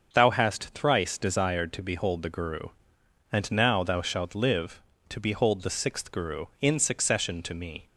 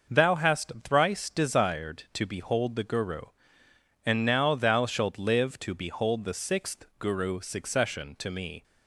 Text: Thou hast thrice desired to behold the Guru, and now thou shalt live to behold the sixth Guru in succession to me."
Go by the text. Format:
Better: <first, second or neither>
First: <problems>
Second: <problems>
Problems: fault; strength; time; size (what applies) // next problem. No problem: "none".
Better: first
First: starts louder than the rest; until 1.1 s; 6.5 dB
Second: starts louder than the rest; noticeable; until 1.2 s; 6 dB // skips "in"; at 7.4 s